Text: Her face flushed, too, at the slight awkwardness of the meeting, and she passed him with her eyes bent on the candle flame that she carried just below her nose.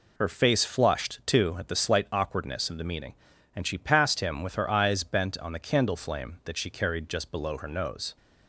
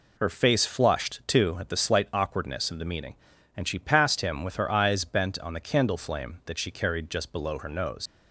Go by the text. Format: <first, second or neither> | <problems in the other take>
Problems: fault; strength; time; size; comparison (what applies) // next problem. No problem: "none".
first | leaves "nose" unfinished; at 8.0 s; 115 ms